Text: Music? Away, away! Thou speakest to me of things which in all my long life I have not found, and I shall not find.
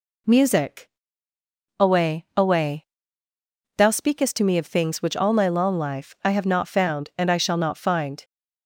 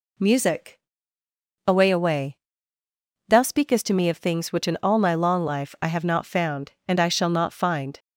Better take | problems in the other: second | skips "in"; at 5.1 s

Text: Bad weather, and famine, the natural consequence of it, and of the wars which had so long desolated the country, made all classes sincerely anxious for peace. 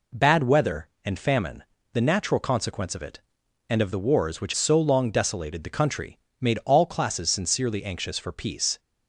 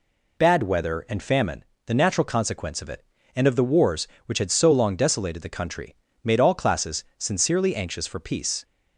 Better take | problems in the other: second | skips "had"; at 4.5 s

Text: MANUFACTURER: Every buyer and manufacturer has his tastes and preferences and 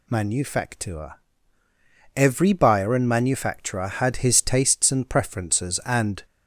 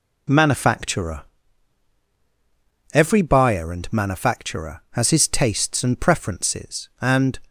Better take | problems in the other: second | says "had" for "has"; at 3.8 s

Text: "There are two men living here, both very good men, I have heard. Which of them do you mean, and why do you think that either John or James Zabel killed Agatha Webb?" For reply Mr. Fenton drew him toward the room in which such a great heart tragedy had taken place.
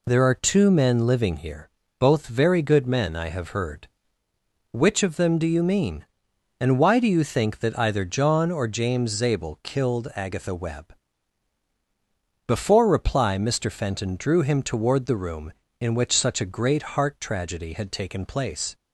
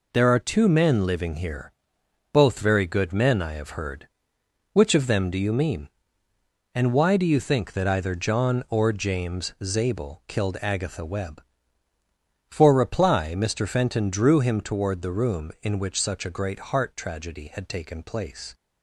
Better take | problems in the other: second | says "Before" for "For"; at 12.4 s // pauses between "great" and "heart"; slight; at 16.8 s; 0.16 s long

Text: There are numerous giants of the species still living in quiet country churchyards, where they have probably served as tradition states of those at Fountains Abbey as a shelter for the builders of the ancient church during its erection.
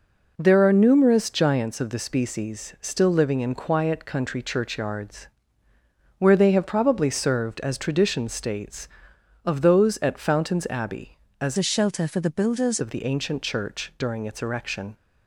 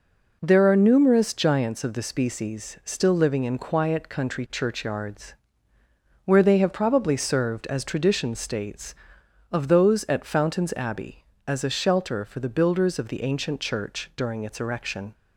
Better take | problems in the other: second | changes voice from "a" to "builders"; from 11.5 to 12.7 s; 1.2 s long

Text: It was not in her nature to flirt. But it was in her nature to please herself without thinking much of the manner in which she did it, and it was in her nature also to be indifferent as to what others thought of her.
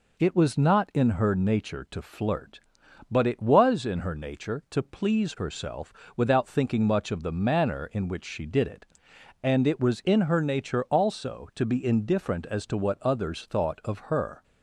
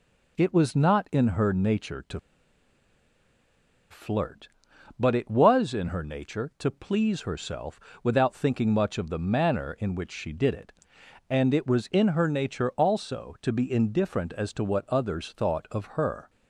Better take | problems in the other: first | pauses between "to" and "flirt"; strong; at 2.1 s; 1.7 s long // pauses between "herself" and "without"; slight; at 7.7 s; 0.24 s long; slight in the first

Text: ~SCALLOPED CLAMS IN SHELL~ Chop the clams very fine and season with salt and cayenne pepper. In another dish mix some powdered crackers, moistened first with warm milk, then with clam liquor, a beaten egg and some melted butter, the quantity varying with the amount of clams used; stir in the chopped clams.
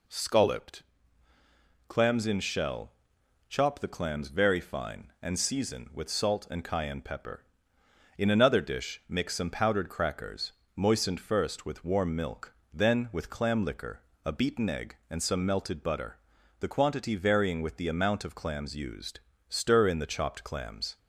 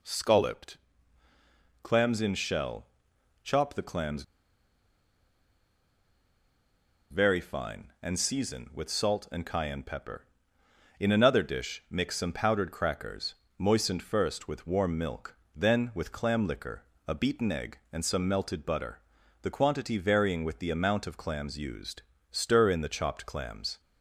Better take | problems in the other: first | pauses between "SCALLOPED" and "CLAMS"; at 0.7 s; 1.0 s long; also in the first // pauses between "clams" and "very"; strong; at 4.2 s; 2.8 s long

